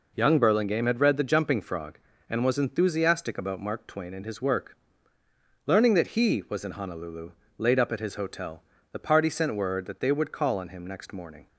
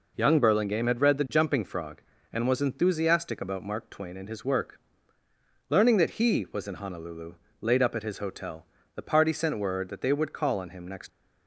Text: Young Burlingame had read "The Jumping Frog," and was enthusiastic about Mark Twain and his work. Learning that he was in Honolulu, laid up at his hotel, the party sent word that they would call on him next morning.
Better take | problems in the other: first | stops before "morning"; at 11.0 s

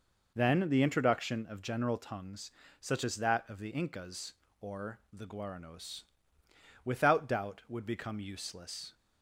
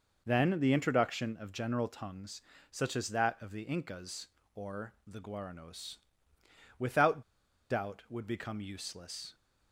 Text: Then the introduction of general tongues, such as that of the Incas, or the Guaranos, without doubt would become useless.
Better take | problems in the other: first | pauses between "without" and "doubt"; noticeable; at 7.2 s; 0.48 s long

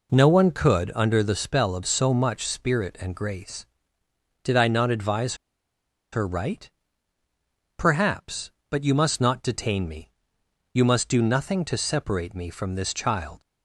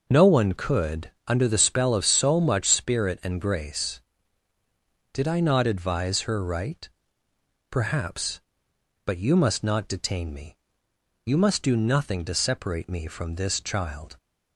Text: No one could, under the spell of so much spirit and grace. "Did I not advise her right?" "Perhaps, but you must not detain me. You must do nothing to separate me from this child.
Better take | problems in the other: second | pauses between "advise" and "her"; noticeable; at 5.3 s; 0.77 s long

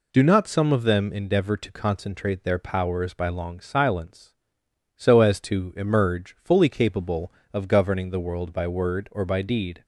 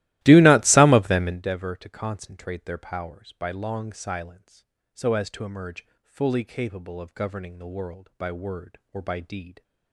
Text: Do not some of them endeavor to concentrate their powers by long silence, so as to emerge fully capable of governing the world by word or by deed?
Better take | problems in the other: first | starts louder than the rest; strong; until 1.5 s; 16.5 dB // pauses between "emerge" and "fully"; slight; at 5.8 s; 0.16 s long

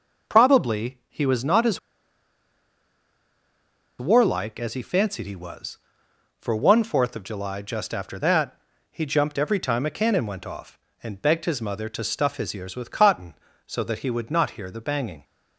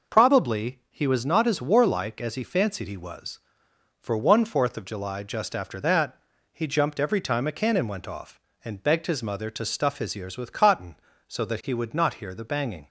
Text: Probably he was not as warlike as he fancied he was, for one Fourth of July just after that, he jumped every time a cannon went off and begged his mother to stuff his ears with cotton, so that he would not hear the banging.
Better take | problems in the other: second | pauses between "as" and "warlike"; strong; at 1.7 s; 2.2 s long

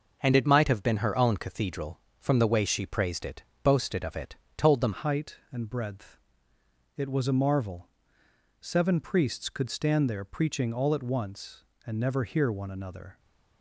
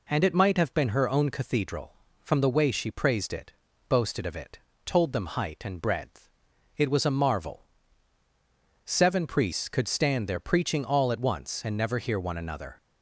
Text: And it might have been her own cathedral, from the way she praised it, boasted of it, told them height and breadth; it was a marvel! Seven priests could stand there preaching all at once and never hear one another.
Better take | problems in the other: second | changes voice at "height"; from 4.9 s on; 8.2 s long

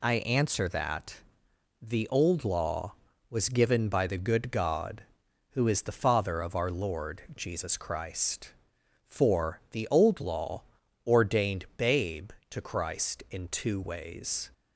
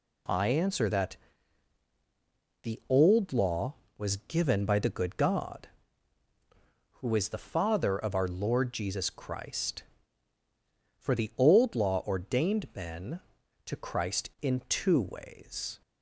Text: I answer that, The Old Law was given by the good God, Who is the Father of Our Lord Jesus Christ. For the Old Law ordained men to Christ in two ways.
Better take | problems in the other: second | pauses between "Law" and "ordained"; at 10.6 s; 0.44 s long // says "babe" for "men"; at 11.7 s

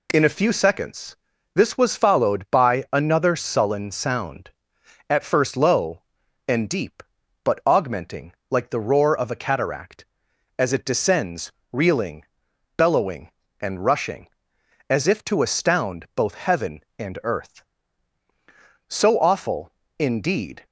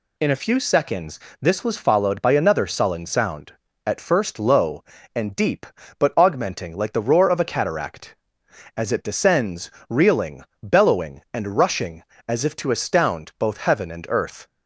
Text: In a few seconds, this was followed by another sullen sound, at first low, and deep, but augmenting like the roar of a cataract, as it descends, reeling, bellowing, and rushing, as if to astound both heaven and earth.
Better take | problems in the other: second | pauses between "augmenting" and "like"; slight; at 8.3 s; 0.16 s long // goes on to say "So awful indeed"; strong; from 18.8 s on; 1.7 s long

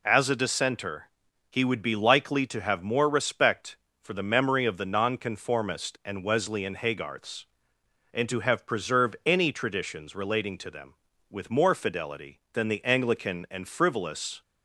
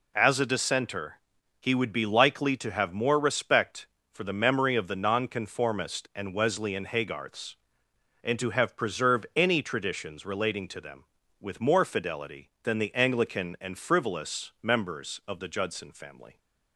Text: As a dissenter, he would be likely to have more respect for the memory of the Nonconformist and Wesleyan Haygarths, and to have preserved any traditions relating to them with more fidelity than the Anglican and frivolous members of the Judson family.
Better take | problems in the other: second | stops before "members of the Judson family"; at 14.4 s

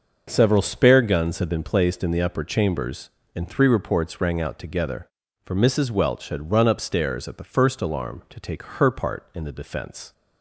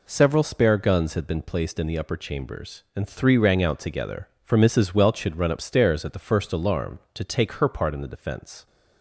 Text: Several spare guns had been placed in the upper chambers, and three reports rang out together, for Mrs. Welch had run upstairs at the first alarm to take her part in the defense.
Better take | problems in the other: first | skips "reports"; at 3.3 s

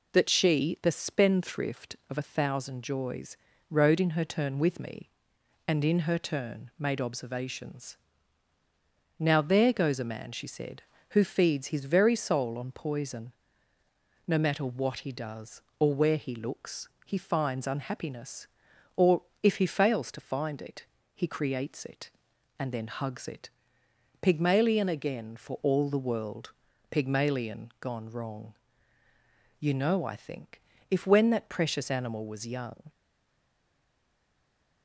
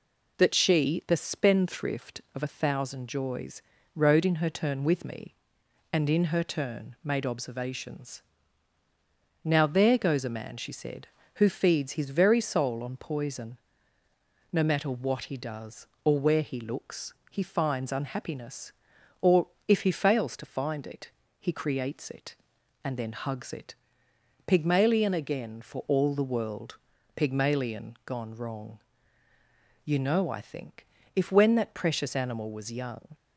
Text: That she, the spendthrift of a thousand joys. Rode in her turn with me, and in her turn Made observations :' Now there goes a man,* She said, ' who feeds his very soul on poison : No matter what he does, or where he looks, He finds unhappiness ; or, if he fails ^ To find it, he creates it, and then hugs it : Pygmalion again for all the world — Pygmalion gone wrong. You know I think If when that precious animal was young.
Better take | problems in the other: second | pauses between "think" and "If"; slight; at 30.5 s; 0.30 s long; slight in the second // stays silent after the last word; noticeable; from 32.8 s on; 2.0 s long

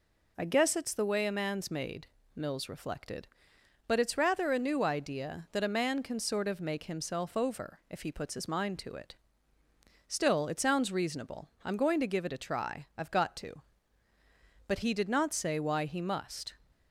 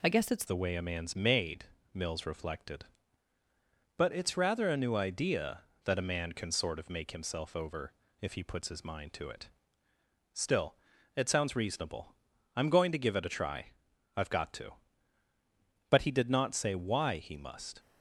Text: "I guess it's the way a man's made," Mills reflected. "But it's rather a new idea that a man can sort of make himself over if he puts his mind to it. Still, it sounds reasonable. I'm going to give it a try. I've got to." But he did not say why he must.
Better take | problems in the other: first | changes voice at "the"; from 0.4 s on; 17.3 s long // pauses between "over" and "if"; slight; at 7.9 s; 0.26 s long

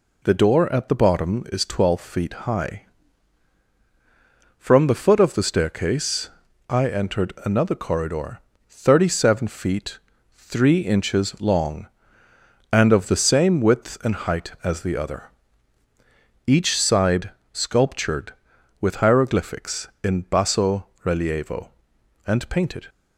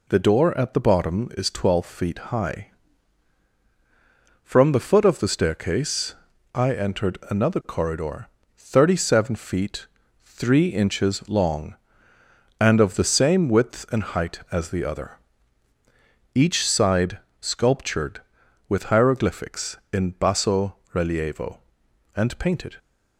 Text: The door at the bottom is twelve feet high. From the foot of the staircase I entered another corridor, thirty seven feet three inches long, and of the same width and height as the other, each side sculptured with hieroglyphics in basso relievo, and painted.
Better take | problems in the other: neither | pauses between "staircase" and "I"; the same in both // pauses between "feet" and "three"; slight; the same in both // pauses between "side" and "sculptured"; slight; the same in both // pauses between "basso" and "relievo"; slight; the same in both

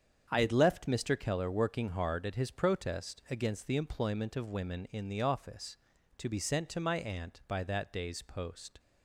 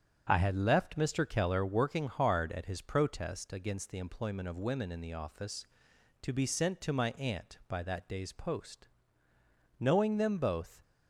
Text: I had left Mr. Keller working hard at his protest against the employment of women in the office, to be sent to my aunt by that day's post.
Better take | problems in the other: first | starts louder than the rest; strong; until 1.3 s; 8 dB; strong in the first // goes on to say "Knowing them both"; noticeable; from 9.7 s on; 1.0 s long

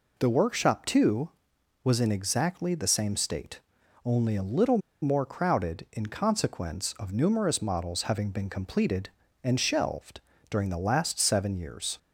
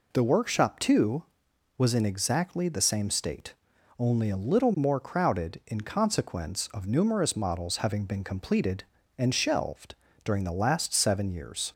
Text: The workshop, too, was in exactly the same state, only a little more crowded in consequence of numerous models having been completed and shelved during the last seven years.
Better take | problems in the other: second | pauses between "little" and "more"; slight; at 4.7 s; 0.23 s long // pauses between "shelved" and "during"; slight; at 10.1 s; 0.28 s long; slight in the second

